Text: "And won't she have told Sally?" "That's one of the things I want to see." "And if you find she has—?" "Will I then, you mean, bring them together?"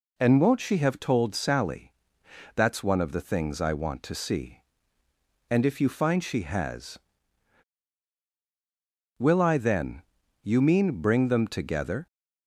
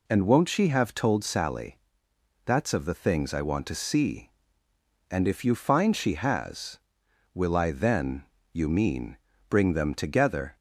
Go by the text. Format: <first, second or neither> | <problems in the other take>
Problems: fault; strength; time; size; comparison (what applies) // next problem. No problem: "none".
first | skips "one"; at 2.7 s